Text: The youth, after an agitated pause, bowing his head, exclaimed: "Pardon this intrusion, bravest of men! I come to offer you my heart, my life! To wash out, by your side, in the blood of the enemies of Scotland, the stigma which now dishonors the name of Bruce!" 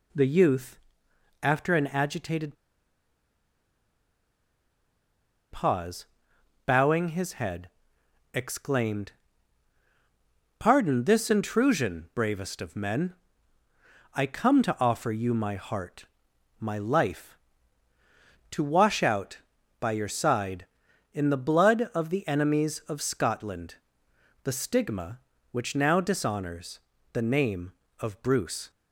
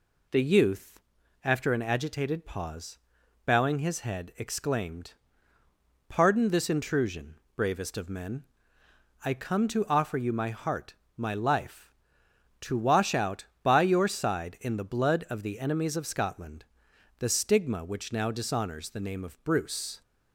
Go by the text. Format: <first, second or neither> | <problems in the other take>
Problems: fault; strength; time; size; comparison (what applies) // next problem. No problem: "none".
second | pauses between "agitated" and "pause"; strong; at 2.5 s; 2.9 s long // pauses between "dishonors" and "the"; slight; at 26.8 s; 0.32 s long